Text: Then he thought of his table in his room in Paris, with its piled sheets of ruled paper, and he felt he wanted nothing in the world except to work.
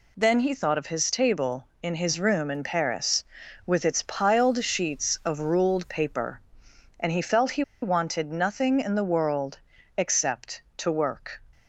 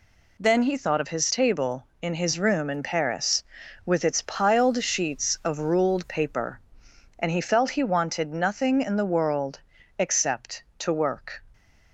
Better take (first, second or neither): second